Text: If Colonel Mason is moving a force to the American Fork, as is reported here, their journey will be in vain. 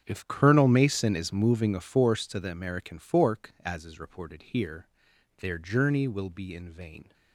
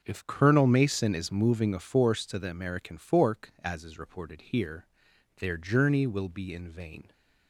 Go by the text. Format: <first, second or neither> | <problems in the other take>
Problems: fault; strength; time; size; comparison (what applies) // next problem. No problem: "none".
second | gets quieter; strong; throughout; 15 dB // starts louder than the rest; strong; until 1.0 s; 8 dB; also in the second